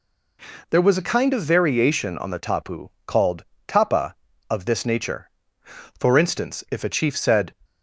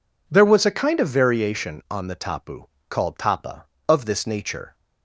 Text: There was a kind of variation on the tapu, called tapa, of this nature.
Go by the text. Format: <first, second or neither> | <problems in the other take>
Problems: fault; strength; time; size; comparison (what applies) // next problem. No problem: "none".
second | pauses between "called" and "tapa"; slight; at 3.4 s; 0.24 s long // goes on to say "For instance if a chief said"; from 5.9 s on; 1.5 s long